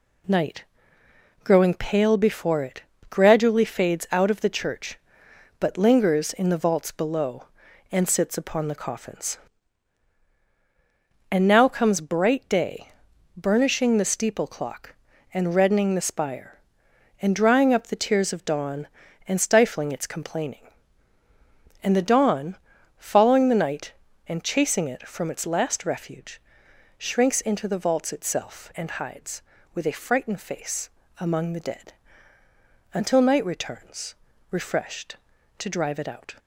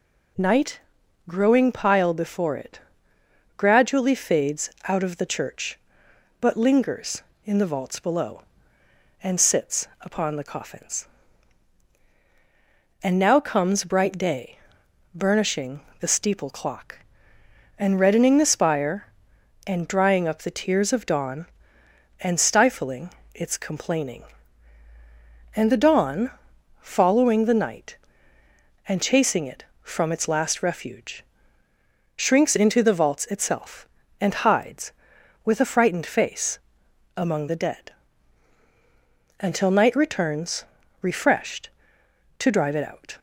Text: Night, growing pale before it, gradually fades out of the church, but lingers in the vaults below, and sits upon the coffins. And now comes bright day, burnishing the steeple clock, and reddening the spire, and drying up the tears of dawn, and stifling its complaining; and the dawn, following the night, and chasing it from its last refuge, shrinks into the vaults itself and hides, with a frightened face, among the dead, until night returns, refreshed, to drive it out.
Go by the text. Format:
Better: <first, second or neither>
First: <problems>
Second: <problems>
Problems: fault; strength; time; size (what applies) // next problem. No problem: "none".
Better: first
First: none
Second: says "pile" for "pale"; at 1.7 s // pauses between "fades" and "out"; slight; at 4.7 s; 0.16 s long // pauses between "sits" and "upon"; slight; at 9.8 s; 0.16 s long // pauses between "burnishing" and "the"; slight; at 15.8 s; 0.18 s long // pauses between "stifling" and "its"; slight; at 23.1 s; 0.24 s long